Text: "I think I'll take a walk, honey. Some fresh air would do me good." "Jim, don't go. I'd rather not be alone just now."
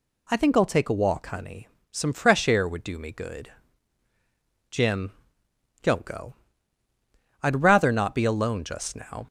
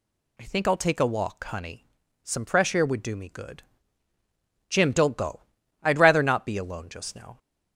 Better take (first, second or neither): neither